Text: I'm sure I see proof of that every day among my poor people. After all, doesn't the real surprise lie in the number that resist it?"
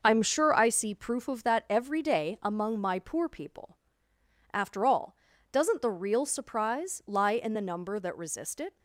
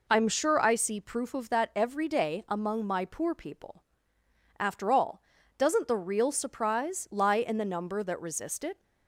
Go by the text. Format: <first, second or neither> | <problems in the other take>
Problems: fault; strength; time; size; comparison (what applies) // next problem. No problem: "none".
second | gets quieter; throughout; 6.5 dB